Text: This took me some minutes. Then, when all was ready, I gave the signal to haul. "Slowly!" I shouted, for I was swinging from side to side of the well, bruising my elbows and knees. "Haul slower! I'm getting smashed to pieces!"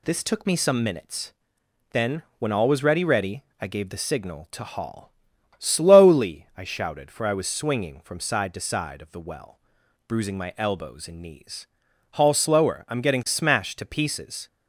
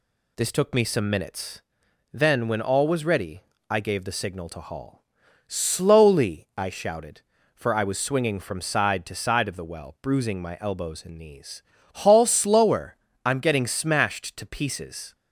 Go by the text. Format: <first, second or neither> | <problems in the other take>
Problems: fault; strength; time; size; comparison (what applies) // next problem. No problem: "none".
second | says "ready" twice; at 3.0 s